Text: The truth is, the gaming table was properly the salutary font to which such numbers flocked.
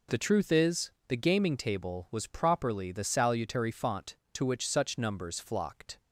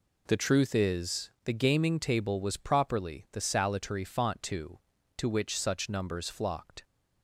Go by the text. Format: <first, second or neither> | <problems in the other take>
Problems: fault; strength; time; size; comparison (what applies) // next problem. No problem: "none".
first | says "to" twice; at 5.1 s